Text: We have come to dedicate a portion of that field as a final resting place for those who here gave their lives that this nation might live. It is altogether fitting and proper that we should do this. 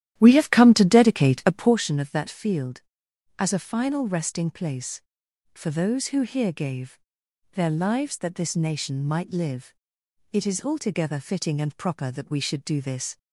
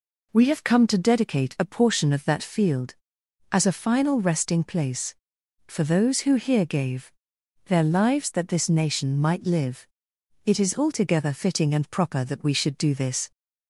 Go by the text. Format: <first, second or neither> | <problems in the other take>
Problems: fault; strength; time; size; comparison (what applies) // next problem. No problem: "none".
second | starts louder than the rest; strong; until 1.8 s; 12 dB // pauses between "gave" and "their"; noticeable; at 6.9 s; 0.54 s long; noticeable in the second